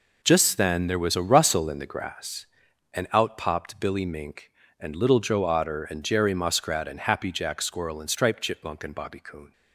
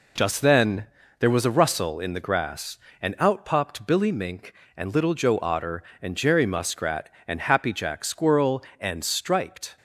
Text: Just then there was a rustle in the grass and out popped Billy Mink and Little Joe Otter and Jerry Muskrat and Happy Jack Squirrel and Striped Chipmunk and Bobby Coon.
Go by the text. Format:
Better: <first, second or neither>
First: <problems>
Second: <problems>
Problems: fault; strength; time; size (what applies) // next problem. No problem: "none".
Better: first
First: none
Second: pauses between "then" and "there"; slight; at 0.8 s; 0.32 s long // stops before "Chipmunk and Bobby Coon"; at 9.7 s